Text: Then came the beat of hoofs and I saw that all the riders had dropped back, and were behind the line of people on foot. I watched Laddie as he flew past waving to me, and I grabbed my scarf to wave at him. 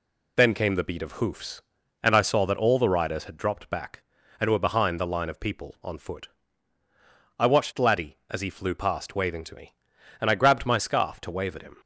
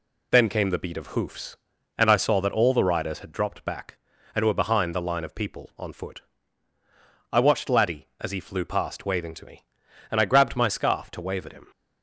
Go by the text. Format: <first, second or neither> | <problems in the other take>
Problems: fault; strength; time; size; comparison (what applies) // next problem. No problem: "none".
neither | none